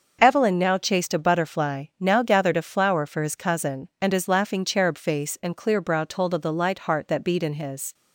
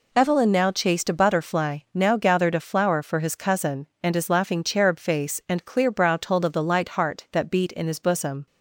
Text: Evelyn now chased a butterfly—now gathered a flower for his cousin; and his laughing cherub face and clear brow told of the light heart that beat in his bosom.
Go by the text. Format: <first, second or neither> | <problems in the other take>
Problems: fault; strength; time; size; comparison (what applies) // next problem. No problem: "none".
second | starts louder than the rest; noticeable; until 1.2 s; 6 dB // stops before "bosom"; at 7.9 s